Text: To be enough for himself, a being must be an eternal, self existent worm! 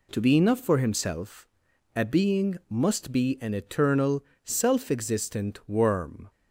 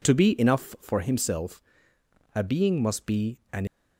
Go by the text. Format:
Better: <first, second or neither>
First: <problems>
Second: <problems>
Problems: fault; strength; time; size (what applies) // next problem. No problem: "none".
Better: first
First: none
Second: pauses between "be" and "an"; slight; at 3.3 s; 0.16 s long // stops before "eternal self existent worm"; at 3.6 s